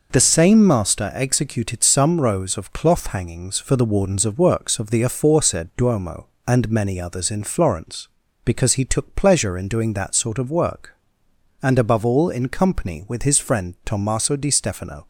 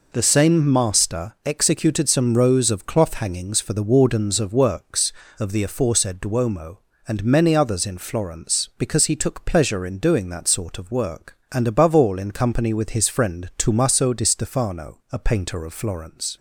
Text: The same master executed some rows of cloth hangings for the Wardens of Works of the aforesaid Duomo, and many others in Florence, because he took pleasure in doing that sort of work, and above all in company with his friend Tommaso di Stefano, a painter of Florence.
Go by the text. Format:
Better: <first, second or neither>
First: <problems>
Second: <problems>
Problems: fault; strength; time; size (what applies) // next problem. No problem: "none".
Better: second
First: stops before "a painter of Florence"; at 15.0 s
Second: none